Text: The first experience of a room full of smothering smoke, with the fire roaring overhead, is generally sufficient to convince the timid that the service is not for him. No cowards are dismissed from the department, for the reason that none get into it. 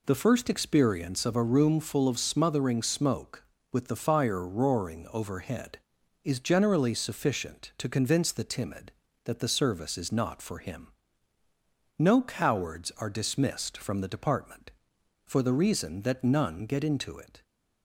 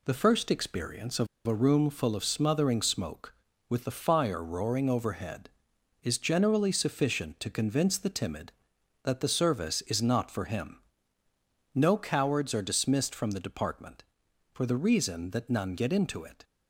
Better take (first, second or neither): first